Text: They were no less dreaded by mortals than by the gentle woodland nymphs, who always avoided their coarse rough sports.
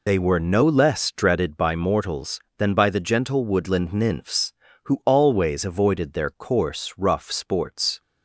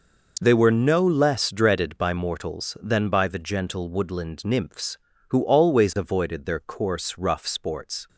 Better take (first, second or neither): second